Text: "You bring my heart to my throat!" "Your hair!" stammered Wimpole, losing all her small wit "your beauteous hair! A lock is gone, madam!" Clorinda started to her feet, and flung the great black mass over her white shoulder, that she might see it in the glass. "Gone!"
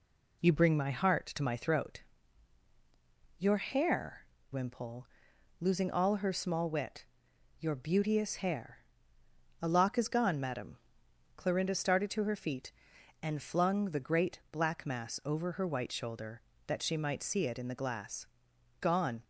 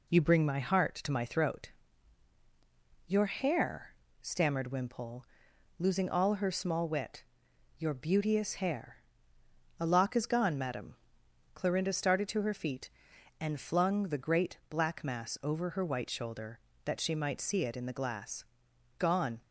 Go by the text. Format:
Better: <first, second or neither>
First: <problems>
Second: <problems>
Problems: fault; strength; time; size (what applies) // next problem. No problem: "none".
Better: second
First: skips "stammered"; at 4.3 s // pauses between "wit" and "your"; noticeable; at 7.0 s; 0.54 s long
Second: pauses between "wit" and "your"; noticeable; at 7.2 s; 0.54 s long